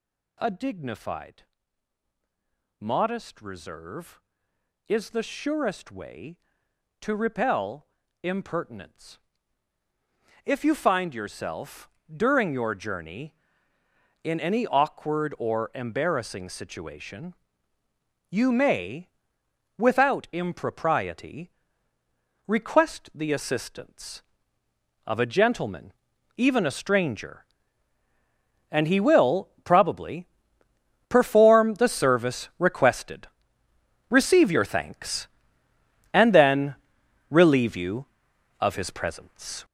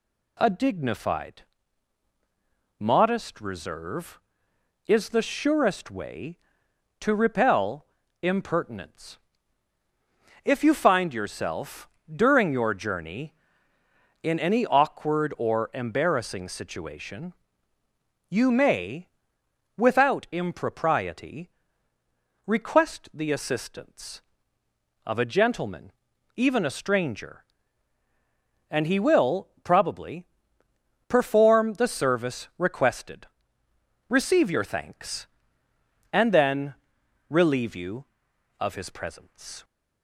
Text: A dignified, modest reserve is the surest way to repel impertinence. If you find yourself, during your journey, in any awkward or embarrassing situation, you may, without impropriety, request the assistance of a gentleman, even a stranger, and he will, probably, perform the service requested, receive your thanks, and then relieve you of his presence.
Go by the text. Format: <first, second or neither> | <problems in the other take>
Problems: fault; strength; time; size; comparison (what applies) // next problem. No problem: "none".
second | gets louder; strong; throughout; 9 dB // pauses between "repel" and "impertinence"; slight; at 7.8 s; 0.36 s long; slight in the second // pauses between "then" and "relieve"; noticeable; at 36.7 s; 0.56 s long; noticeable in the second